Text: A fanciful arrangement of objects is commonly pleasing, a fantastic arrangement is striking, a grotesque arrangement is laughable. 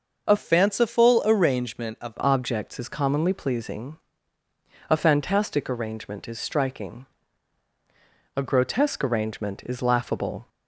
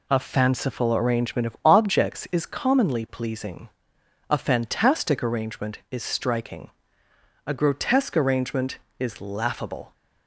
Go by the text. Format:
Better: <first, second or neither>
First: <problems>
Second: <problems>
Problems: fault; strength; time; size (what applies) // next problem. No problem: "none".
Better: second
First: starts louder than the rest; until 1.3 s; 6.5 dB // changes voice from "fanciful" to "of"; from 0.3 to 2.1 s; 1.8 s long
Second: none